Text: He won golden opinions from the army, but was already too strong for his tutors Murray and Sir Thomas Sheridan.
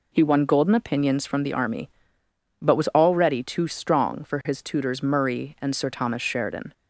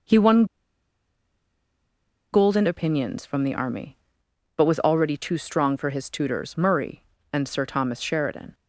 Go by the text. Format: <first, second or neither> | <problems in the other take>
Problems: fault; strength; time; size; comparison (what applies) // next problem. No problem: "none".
first | pauses between "won" and "golden"; strong; at 0.4 s; 1.8 s long